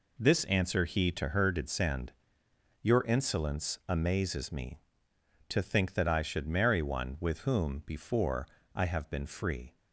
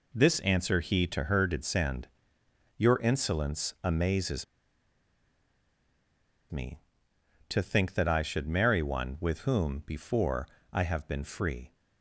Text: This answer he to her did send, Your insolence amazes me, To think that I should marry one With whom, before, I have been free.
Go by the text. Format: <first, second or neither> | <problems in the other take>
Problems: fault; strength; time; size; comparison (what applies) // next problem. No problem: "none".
first | pauses between "amazes" and "me"; strong; at 4.4 s; 2.0 s long